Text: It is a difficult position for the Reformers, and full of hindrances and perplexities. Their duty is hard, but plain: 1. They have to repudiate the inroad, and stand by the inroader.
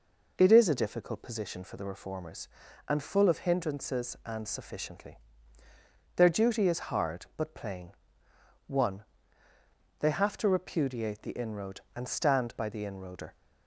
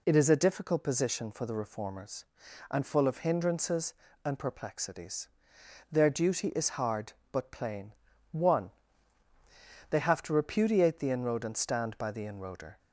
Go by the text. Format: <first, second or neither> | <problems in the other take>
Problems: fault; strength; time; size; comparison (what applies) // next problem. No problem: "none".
second | says "sufficiently" for "perplexities"; at 4.4 s